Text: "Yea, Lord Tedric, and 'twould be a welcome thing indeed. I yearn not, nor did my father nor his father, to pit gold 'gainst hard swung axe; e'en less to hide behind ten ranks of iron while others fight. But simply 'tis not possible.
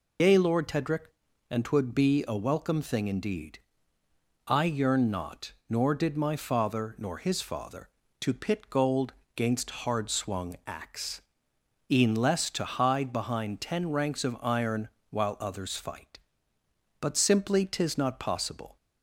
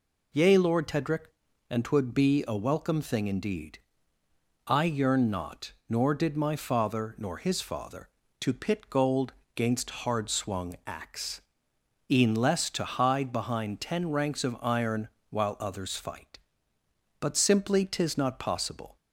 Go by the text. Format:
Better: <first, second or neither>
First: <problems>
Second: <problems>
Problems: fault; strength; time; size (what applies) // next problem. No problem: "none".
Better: second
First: loses the start of "Yea"; at 0.1 s; 60 ms // pauses between "gold" and "gainst"; slight; at 9.1 s; 0.22 s long // pauses between "iron" and "while"; slight; at 14.8 s; 0.18 s long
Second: pauses between "gold" and "gainst"; slight; at 9.3 s; 0.22 s long // pauses between "iron" and "while"; slight; at 15.0 s; 0.18 s long